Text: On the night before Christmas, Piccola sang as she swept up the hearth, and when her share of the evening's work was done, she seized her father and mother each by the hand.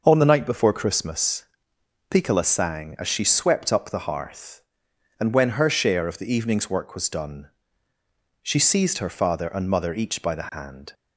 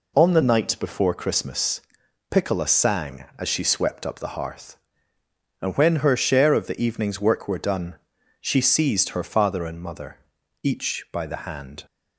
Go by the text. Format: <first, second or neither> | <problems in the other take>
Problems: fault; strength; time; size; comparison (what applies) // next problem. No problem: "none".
first | says "were" for "was"; at 7.4 s // pauses between "mother" and "each"; at 10.1 s; 0.44 s long